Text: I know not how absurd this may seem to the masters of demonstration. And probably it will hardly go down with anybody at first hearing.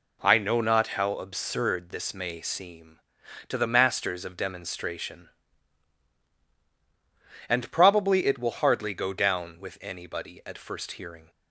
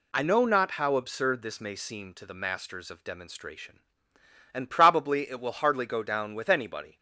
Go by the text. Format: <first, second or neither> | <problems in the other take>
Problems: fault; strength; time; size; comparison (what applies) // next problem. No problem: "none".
first | stops before "at first hearing"; at 6.9 s